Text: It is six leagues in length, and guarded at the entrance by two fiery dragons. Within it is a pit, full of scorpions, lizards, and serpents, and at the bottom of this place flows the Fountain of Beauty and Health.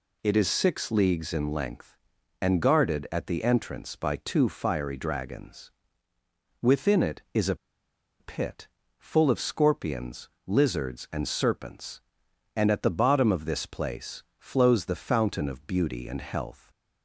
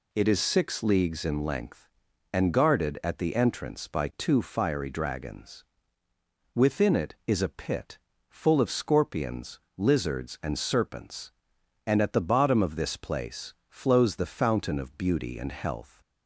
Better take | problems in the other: second | pauses between "a" and "pit"; noticeable; at 7.5 s; 0.64 s long // pauses between "place" and "flows"; slight; at 14.2 s; 0.16 s long; slight in the second

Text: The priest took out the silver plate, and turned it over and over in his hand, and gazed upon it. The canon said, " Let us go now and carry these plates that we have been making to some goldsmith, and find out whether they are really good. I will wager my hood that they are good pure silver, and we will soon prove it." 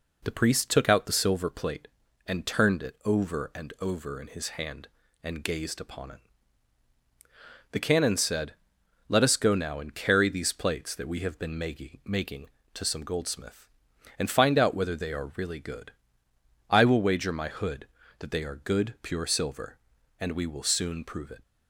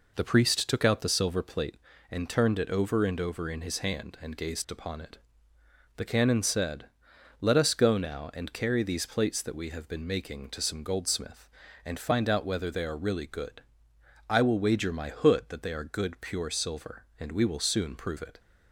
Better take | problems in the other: second | says "making" twice; at 12.0 s

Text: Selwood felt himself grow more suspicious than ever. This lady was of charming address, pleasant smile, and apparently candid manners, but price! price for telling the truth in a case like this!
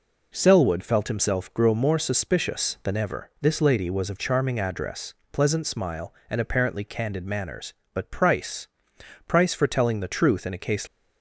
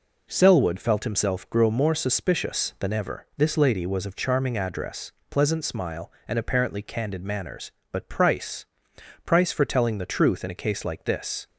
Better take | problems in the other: second | stops before "like this"; at 10.8 s

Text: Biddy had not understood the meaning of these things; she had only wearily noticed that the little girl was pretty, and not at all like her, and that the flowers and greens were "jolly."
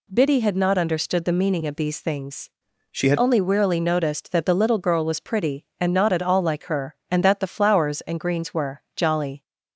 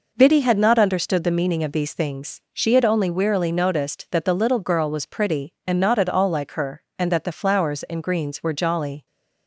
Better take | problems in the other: second | changes voice from "she" to "had"; from 2.9 to 3.1 s; 0.2 s long

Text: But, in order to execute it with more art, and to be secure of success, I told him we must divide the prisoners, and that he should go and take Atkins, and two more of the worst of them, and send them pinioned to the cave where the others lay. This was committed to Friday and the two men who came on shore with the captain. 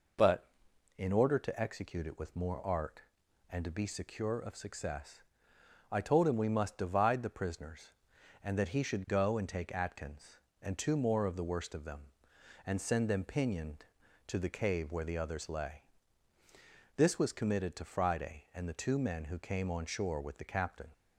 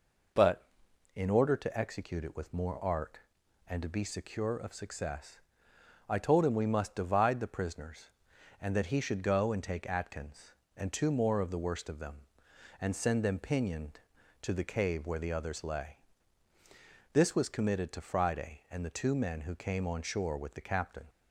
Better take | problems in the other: neither | none

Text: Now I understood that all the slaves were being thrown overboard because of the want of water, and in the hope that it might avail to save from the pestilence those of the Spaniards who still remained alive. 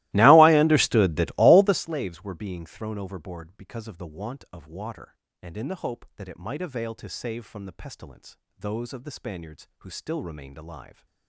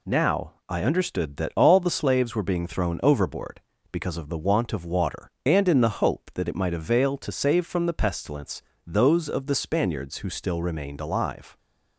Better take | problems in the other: second | starts louder than the rest; strong; until 1.9 s; 19.5 dB // pauses between "pestilence" and "those"; slight; at 8.3 s; 0.22 s long; slight in the second

